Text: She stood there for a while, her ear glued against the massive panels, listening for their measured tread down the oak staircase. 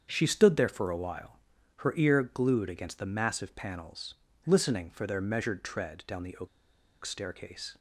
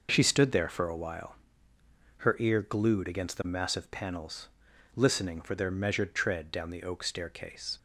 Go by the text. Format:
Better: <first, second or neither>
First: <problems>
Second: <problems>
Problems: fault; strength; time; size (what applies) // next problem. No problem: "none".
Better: second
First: starts louder than the rest; strong; until 1.1 s; 7.5 dB // pauses between "oak" and "staircase"; noticeable; at 6.4 s; 0.57 s long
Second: none